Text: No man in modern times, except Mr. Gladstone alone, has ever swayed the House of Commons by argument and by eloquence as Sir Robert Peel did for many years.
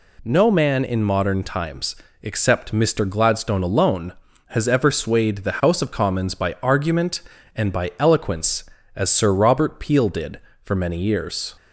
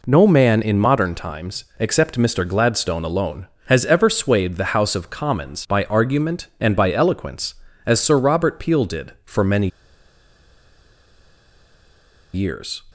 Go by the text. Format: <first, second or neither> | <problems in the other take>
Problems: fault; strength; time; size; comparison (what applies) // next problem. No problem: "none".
first | pauses between "many" and "years"; strong; at 9.6 s; 2.6 s long